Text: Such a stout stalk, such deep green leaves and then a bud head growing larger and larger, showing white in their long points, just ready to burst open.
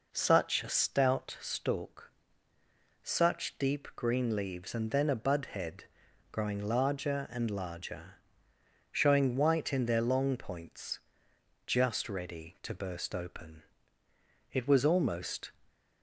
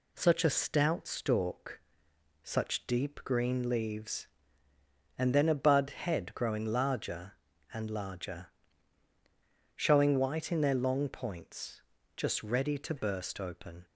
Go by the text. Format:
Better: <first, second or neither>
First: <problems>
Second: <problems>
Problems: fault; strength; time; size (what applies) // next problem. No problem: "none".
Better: second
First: pauses between "head" and "growing"; noticeable; at 5.8 s; 0.48 s long // goes on to say "It was almost"; noticeable; from 14.5 s on; 1.0 s long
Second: none